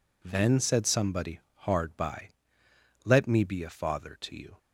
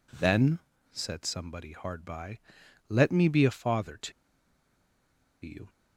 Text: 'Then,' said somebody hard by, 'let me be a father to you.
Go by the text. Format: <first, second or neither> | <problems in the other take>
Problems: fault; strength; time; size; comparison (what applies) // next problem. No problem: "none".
first | pauses between "to" and "you"; strong; at 4.1 s; 1.3 s long